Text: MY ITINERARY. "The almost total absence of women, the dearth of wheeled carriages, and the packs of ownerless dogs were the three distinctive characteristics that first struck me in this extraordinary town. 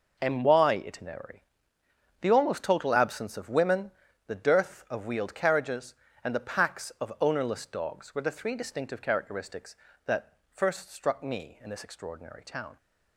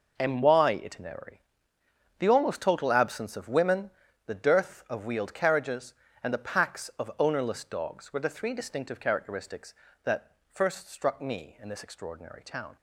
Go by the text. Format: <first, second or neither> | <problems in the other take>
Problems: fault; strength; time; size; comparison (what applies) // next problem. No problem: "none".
neither | pauses between "that" and "first"; slight; the same in both